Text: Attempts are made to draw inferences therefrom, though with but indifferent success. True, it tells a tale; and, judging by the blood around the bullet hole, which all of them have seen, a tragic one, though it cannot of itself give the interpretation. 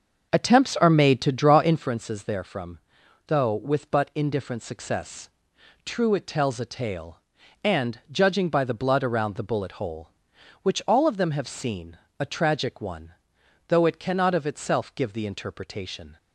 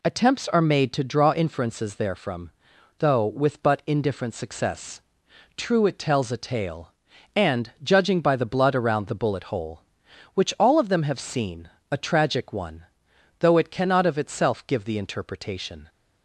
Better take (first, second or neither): second